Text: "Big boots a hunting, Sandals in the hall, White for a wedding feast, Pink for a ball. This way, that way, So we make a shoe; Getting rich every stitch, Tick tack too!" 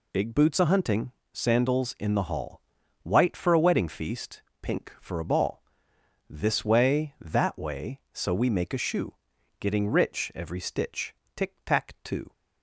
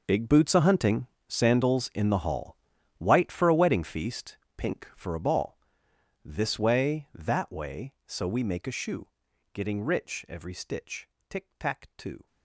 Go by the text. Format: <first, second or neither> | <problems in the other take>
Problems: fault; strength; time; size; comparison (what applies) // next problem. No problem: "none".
first | gets quieter; strong; throughout; 15.5 dB